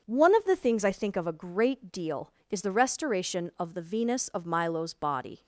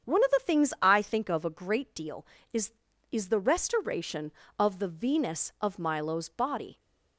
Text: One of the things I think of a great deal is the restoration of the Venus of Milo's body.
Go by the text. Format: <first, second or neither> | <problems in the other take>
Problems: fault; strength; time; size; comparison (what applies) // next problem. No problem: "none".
first | starts louder than the rest; strong; until 1.1 s; 8 dB; also in the first // says "is" twice; at 3.1 s